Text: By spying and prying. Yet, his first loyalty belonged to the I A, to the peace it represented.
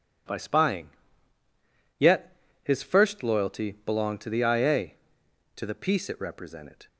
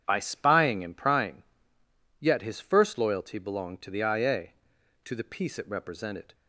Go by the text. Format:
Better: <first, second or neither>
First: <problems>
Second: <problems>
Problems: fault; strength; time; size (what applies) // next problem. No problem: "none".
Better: second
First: skips "and prying"; at 1.4 s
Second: none